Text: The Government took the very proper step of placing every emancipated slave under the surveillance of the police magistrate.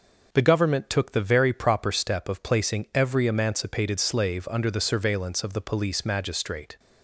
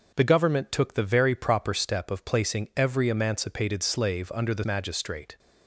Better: first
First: none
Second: starts louder than the rest; noticeable; until 1.1 s; 6 dB // skips "surveillance of the police"; at 4.6 s

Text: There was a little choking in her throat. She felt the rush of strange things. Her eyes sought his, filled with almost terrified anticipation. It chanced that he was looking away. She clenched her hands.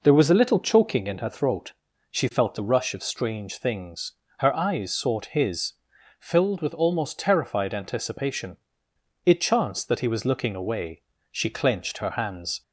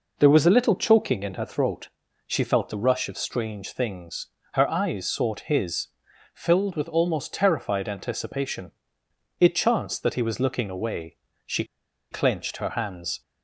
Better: first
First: none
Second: pauses between "She" and "clenched"; noticeable; at 11.6 s; 0.46 s long

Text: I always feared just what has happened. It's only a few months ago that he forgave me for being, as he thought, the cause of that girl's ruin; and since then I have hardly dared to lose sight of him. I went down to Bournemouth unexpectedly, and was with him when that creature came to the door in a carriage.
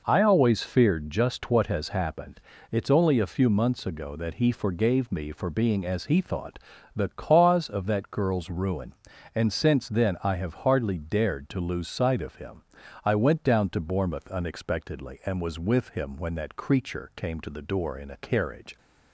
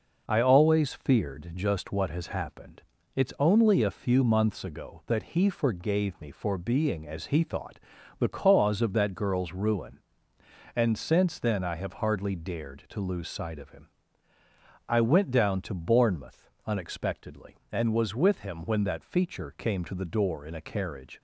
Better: first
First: none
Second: pauses between "Bournemouth" and "unexpectedly"; slight; at 16.4 s; 0.18 s long // says "feature" for "creature"; at 19.0 s

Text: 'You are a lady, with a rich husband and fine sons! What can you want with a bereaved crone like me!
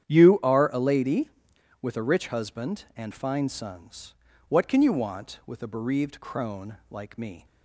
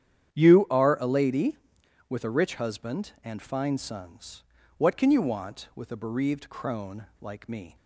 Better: neither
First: starts louder than the rest; strong; until 1.1 s; 9.5 dB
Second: starts louder than the rest; strong; until 1.4 s; 9.5 dB

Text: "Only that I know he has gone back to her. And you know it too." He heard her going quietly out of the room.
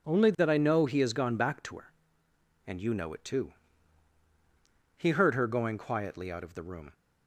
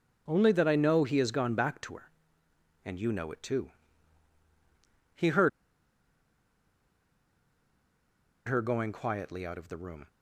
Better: first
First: none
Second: pauses between "heard" and "her"; strong; at 5.4 s; 2.9 s long

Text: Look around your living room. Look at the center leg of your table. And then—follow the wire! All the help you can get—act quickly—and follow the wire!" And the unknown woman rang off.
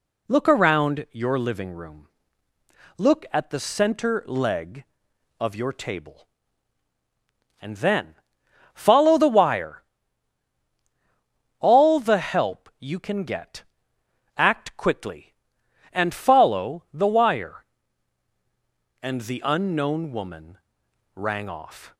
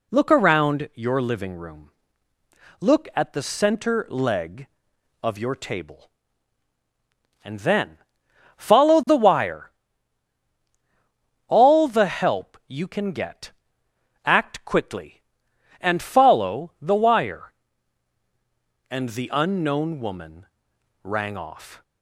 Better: neither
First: pauses between "woman" and "rang"; noticeable; at 20.5 s; 0.56 s long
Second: pauses between "woman" and "rang"; noticeable; at 20.4 s; 0.56 s long

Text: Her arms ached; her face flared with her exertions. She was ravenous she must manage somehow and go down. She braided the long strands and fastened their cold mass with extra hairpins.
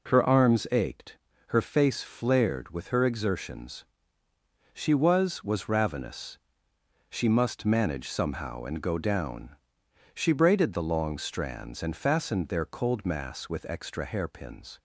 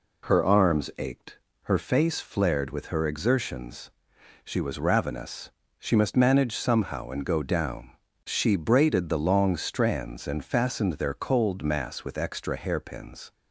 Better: second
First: says "was" twice; at 5.4 s // pauses between "ravenous" and "she"; noticeable; at 6.3 s; 0.70 s long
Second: pauses between "ravenous" and "she"; slight; at 5.5 s; 0.28 s long

